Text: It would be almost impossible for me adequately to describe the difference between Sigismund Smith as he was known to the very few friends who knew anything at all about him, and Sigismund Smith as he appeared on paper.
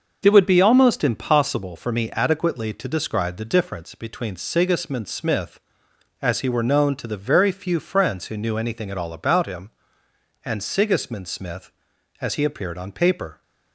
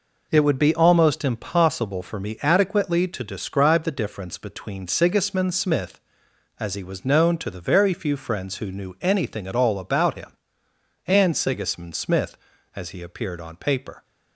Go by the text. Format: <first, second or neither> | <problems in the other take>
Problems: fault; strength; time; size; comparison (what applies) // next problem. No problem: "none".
second | starts louder than the rest; noticeable; until 1.2 s; 6 dB // says "were" for "was"; at 6.4 s